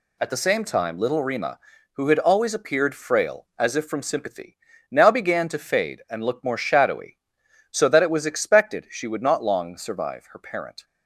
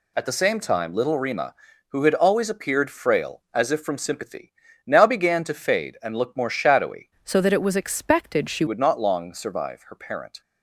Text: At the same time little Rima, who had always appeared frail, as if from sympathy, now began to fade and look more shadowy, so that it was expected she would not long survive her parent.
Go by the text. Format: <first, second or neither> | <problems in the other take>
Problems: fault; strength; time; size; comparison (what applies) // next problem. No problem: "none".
first | changes voice from "so" to "she"; from 7.2 to 8.6 s; 1.4 s long